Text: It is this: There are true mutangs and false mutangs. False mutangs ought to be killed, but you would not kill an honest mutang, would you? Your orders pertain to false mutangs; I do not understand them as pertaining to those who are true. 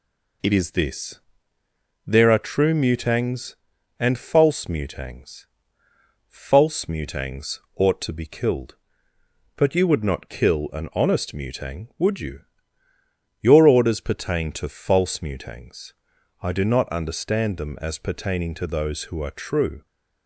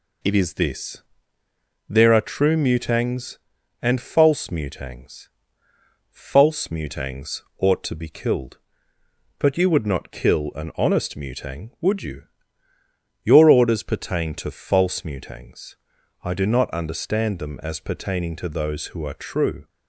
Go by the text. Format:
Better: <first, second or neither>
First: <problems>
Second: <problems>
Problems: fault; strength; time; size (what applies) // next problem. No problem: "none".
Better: neither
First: pauses between "mutangs" and "ought"; slight; at 7.5 s; 0.16 s long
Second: pauses between "mutangs" and "ought"; slight; at 7.4 s; 0.16 s long